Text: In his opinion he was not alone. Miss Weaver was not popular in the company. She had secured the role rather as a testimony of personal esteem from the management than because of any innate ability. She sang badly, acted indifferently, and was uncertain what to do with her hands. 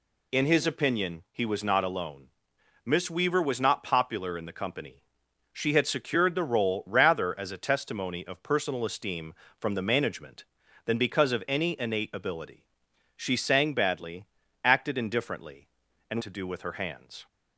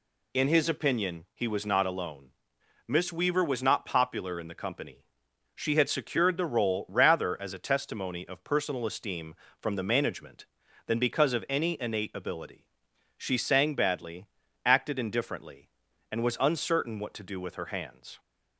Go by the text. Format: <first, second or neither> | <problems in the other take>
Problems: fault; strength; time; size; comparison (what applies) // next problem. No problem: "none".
second | skips "was uncertain what"; at 16.2 s